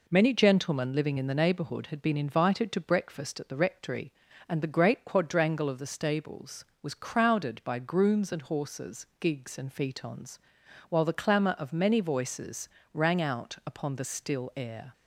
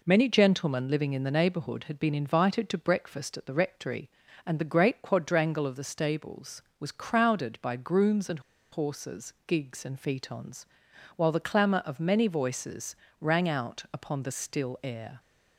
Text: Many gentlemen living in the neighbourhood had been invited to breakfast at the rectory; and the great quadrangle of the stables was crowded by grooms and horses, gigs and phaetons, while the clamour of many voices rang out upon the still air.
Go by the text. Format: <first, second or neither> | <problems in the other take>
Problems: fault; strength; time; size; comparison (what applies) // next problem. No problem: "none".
first | pauses between "and" and "horses"; slight; at 8.3 s; 0.32 s long // pauses between "voices" and "rang"; slight; at 12.9 s; 0.24 s long; slight in the first